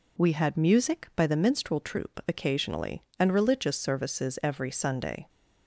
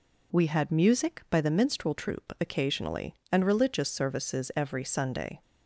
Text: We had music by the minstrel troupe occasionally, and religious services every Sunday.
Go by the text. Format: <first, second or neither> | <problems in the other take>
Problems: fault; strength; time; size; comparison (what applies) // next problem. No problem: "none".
neither | none